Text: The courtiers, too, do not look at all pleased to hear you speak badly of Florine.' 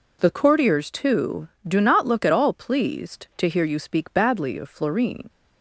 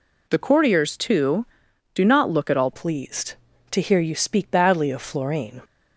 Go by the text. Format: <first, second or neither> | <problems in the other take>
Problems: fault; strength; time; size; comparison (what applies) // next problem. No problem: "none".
first | changes voice at "pleased"; from 2.7 s on; 2.9 s long